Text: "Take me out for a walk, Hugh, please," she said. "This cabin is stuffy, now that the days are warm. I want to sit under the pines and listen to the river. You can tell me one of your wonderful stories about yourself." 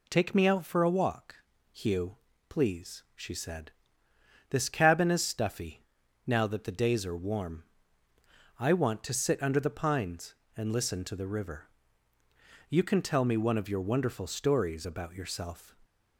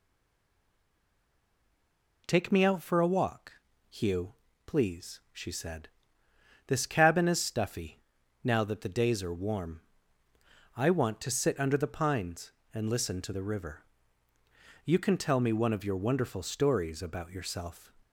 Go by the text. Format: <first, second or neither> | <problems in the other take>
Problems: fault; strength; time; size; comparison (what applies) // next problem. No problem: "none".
first | stays silent before the first word; until 2.2 s; 2.2 s long